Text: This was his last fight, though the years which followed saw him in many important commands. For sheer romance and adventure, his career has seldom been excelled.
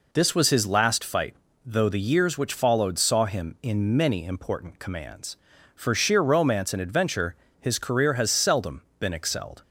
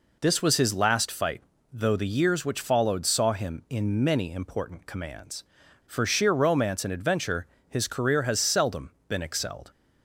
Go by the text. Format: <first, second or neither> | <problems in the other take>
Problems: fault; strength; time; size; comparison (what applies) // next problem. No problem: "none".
neither | pauses between "seldom" and "been"; slight; the same in both